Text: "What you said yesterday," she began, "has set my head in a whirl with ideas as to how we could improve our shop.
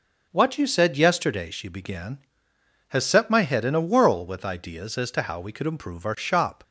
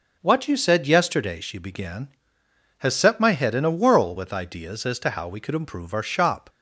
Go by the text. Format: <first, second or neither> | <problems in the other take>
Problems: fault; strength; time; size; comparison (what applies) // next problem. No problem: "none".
neither | none